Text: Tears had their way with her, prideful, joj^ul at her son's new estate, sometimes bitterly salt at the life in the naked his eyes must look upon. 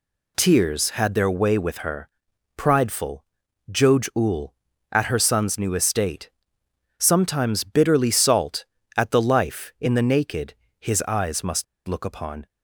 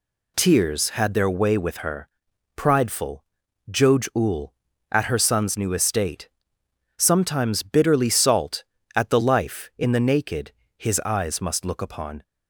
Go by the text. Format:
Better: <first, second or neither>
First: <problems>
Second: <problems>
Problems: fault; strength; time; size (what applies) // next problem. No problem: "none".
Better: second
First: pauses between "naked" and "his"; slight; at 10.5 s; 0.24 s long // pauses between "must" and "look"; slight; at 11.6 s; 0.22 s long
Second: pauses between "naked" and "his"; slight; at 10.5 s; 0.24 s long